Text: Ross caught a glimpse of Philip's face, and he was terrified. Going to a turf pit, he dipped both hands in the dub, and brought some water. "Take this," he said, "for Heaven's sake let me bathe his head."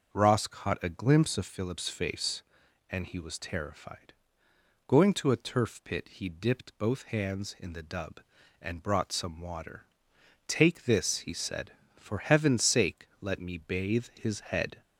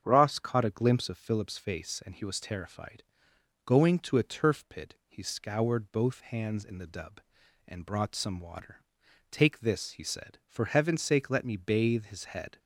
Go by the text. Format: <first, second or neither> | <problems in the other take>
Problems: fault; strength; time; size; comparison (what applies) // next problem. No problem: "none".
first | starts louder than the rest; strong; until 1.0 s; 7.5 dB; also in the first // says "scoured" for "dipped"; at 5.2 s